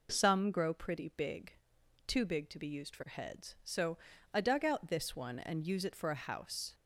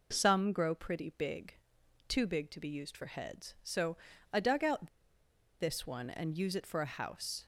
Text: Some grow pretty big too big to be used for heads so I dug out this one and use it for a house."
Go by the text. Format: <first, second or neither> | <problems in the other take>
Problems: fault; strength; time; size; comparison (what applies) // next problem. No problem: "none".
first | pauses between "big" and "too"; noticeable; at 1.5 s; 0.54 s long; noticeable in the first // pauses between "so" and "I"; at 3.9 s; 0.38 s long; also in the first // pauses between "out" and "this"; noticeable; at 4.8 s; 0.72 s long